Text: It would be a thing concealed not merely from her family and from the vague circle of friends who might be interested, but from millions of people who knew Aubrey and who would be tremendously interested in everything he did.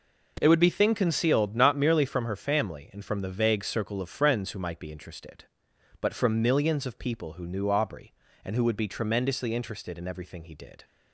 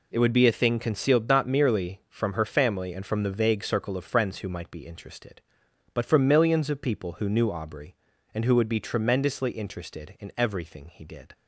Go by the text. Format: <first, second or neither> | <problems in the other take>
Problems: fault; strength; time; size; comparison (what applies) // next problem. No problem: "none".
second | skips "a"; at 0.7 s